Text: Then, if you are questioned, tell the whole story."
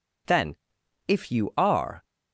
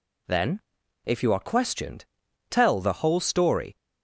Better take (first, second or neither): second